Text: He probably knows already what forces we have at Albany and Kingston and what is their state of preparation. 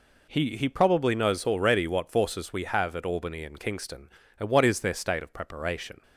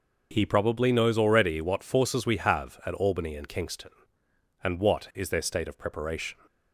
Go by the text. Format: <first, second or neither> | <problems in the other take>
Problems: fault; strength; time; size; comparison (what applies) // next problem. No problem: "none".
second | says "He" twice; at 0.5 s